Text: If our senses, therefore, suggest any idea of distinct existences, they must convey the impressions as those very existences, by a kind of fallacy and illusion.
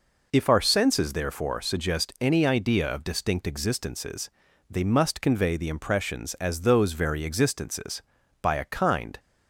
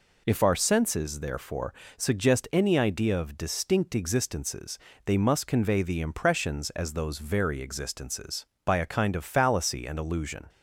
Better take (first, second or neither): second